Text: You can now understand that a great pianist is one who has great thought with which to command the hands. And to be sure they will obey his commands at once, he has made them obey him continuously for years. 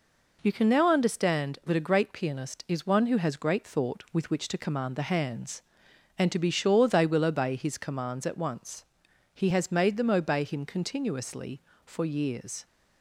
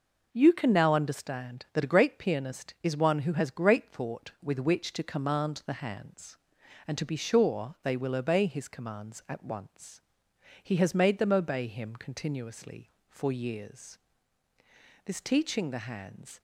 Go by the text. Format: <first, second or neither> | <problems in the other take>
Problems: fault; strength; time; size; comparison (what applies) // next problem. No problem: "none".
first | goes on to say "This teaching the hands"; from 15.0 s on; 1.3 s long